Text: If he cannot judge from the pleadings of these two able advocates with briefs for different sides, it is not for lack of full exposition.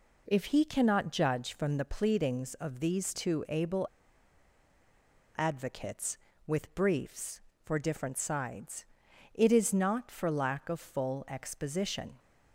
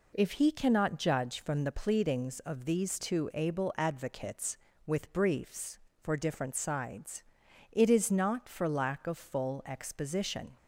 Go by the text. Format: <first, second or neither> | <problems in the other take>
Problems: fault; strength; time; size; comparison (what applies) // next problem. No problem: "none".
second | pauses between "able" and "advocates"; strong; at 3.8 s; 1.5 s long